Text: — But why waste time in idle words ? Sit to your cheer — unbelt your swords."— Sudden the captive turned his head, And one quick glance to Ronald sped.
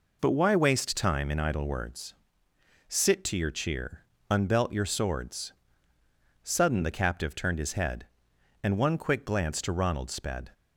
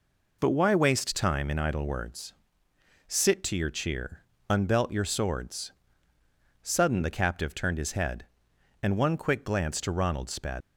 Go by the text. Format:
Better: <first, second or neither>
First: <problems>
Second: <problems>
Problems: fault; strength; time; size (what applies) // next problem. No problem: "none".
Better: first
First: none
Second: leaves "sped" unfinished; at 10.6 s; 120 ms